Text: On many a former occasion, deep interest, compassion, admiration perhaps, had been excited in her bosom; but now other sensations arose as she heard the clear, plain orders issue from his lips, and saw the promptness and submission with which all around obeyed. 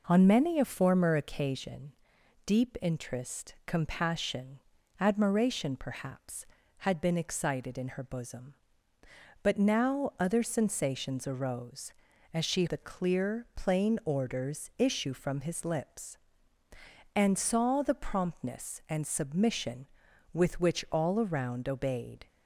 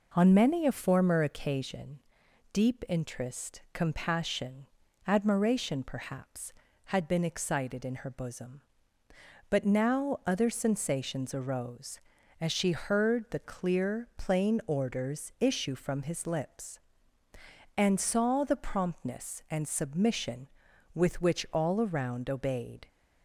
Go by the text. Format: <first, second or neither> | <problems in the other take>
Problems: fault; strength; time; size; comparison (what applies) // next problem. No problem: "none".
second | skips "heard"; at 12.6 s